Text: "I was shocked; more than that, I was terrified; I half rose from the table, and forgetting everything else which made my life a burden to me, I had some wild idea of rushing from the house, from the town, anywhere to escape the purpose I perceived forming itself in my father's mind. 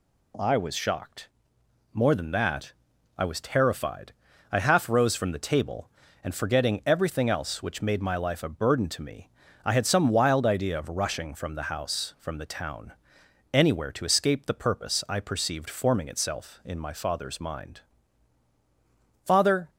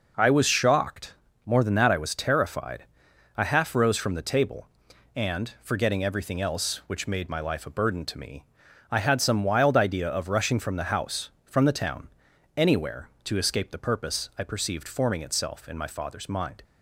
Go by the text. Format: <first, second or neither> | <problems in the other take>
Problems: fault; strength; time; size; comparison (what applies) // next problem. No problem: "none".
second | goes on to say "Father"; slight; from 19.2 s on; 0.46 s long